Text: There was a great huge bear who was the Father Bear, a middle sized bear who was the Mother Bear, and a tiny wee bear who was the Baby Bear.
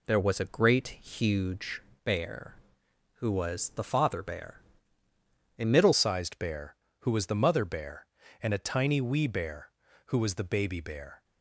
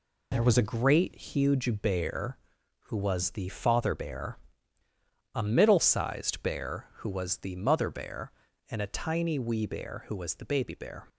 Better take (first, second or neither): second